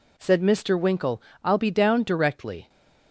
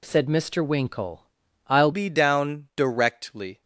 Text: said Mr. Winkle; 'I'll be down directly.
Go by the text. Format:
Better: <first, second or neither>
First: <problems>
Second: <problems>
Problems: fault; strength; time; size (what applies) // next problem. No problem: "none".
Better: first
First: none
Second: changes voice at "be"; from 1.9 s on; 1.7 s long